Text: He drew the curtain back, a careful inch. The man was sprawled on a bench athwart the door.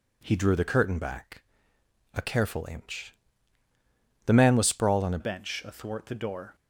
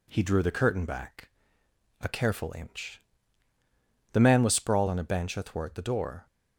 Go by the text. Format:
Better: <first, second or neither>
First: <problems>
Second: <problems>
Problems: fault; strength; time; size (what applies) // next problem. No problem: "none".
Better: second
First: changes voice at "bench"; from 5.2 s on; 1.3 s long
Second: none